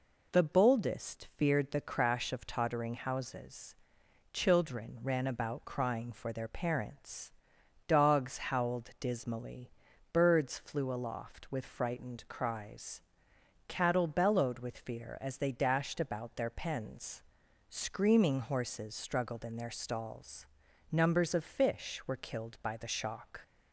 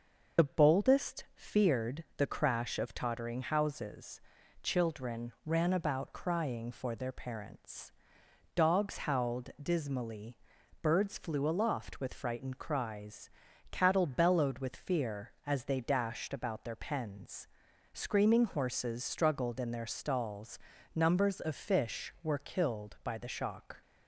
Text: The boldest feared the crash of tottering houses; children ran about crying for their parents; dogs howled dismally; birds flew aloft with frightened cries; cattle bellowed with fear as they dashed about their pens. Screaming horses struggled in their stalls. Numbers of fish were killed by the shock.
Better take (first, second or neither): first